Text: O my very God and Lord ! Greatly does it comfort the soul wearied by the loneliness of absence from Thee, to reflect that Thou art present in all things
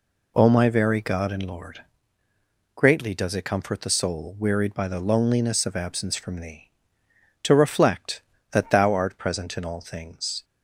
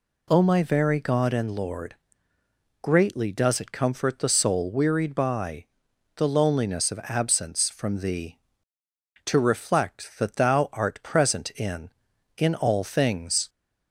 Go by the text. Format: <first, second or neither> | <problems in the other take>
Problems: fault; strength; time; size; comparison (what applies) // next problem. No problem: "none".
first | pauses between "by" and "the"; noticeable; at 5.6 s; 0.52 s long // says "in" twice; at 12.3 s